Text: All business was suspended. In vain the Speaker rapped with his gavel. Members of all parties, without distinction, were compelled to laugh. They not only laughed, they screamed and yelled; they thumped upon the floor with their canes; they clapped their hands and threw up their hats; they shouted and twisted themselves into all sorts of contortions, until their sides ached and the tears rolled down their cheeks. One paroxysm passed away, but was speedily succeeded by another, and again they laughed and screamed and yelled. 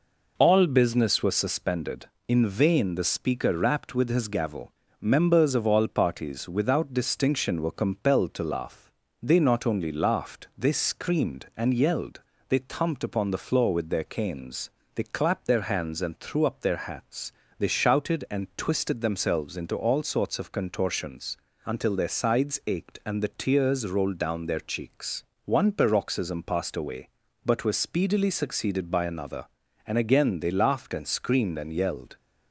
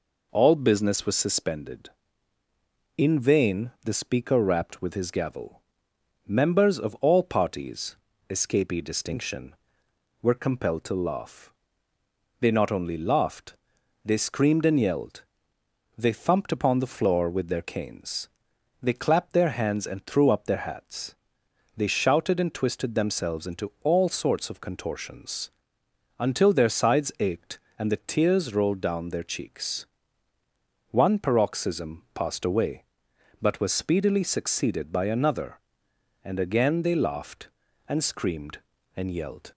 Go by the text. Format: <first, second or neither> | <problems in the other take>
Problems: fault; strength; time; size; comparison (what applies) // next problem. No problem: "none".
first | says "escapee" for "without"; at 8.2 s